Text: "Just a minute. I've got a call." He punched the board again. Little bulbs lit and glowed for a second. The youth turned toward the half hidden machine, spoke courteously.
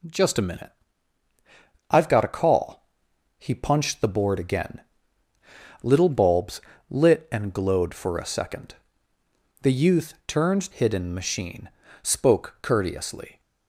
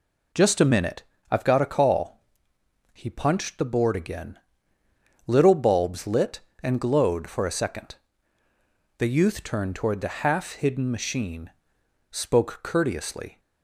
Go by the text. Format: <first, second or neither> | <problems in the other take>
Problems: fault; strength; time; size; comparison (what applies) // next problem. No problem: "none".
second | pauses between "bulbs" and "lit"; slight; at 6.6 s; 0.28 s long // skips "toward the half"; at 10.7 s